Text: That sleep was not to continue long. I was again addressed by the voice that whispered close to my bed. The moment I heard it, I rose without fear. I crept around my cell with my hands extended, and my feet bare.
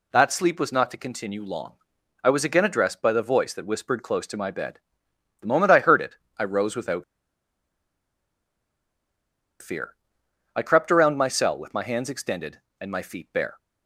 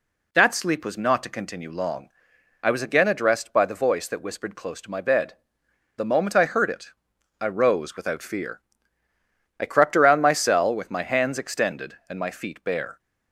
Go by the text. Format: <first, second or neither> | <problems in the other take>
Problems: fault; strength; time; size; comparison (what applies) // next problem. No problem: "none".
second | pauses between "without" and "fear"; strong; at 7.0 s; 2.5 s long